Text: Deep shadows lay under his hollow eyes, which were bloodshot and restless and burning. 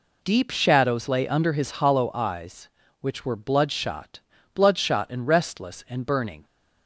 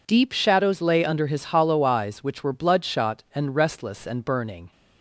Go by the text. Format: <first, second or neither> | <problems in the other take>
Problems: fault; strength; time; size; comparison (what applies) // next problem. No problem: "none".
second | says "bloodshot" twice; at 4.5 s